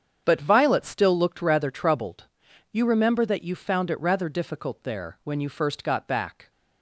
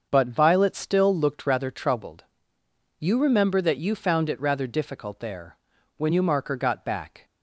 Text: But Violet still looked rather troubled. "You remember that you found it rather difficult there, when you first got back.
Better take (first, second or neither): first